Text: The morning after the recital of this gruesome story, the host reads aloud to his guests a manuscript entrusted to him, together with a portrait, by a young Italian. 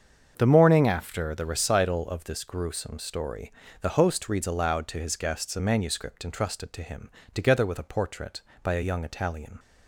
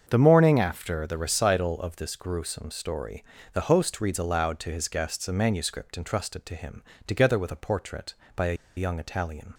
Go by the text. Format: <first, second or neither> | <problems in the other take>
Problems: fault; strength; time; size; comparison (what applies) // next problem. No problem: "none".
first | starts louder than the rest; until 1.1 s; 7 dB; also in the first // pauses between "a" and "young"; slight; at 8.5 s; 0.23 s long